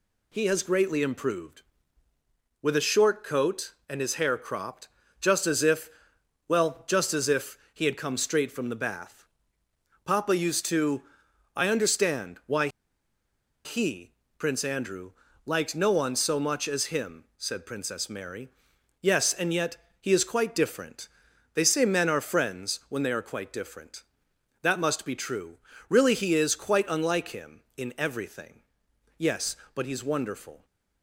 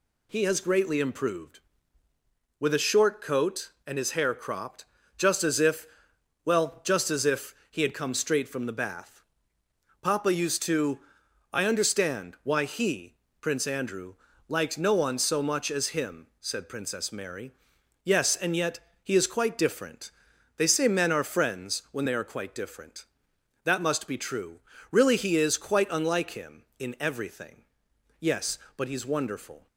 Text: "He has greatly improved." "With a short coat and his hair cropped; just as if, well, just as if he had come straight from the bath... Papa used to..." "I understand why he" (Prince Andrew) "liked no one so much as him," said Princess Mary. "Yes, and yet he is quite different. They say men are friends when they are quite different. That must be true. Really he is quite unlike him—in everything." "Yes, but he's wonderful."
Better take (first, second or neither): second